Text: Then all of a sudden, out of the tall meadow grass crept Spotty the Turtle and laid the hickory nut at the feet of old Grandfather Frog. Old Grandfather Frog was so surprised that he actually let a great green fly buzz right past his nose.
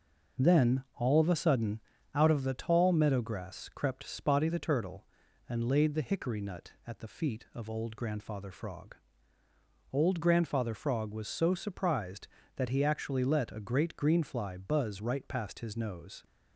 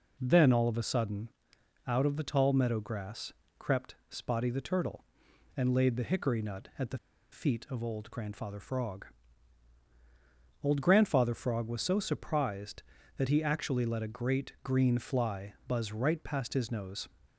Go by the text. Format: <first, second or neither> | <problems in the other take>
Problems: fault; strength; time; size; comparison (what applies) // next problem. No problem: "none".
first | pauses between "grass" and "crept"; slight; at 3.3 s; 0.26 s long // pauses between "the" and "feet"; slight; at 6.9 s; 0.33 s long